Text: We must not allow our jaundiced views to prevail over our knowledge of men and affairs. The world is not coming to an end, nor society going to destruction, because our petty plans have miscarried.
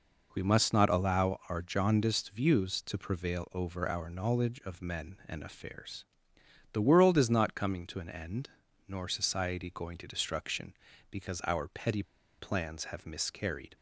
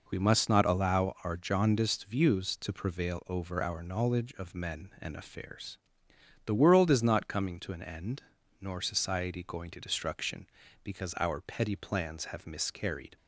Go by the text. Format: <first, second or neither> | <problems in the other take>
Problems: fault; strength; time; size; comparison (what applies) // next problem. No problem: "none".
second | pauses between "petty" and "plans"; slight; at 12.0 s; 0.35 s long